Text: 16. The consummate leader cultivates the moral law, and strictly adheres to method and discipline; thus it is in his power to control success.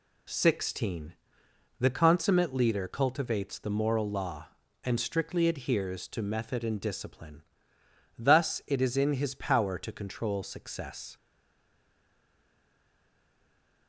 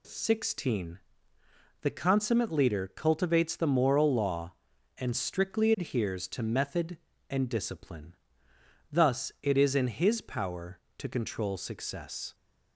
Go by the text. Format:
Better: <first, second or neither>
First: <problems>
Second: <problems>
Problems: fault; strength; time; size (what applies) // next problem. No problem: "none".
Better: second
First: stays silent after the last word; strong; from 11.1 s on; 2.7 s long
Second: none